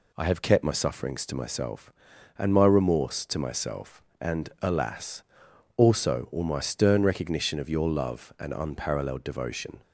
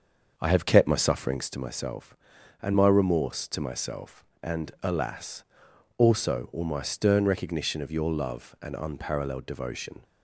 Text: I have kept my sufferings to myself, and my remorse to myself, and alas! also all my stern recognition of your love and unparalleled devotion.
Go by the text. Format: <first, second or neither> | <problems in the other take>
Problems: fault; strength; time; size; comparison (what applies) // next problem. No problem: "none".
first | starts louder than the rest; until 1.5 s; 6.5 dB